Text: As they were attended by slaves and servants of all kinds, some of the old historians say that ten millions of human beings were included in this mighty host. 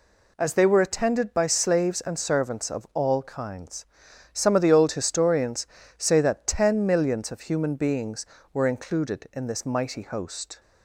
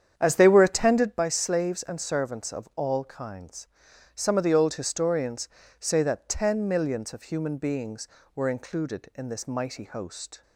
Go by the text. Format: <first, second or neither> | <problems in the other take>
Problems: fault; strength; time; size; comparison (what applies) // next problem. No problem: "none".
first | starts louder than the rest; strong; until 1.3 s; 8.5 dB // pauses between "historians" and "say"; slight; at 5.4 s; 0.28 s long; slight in the first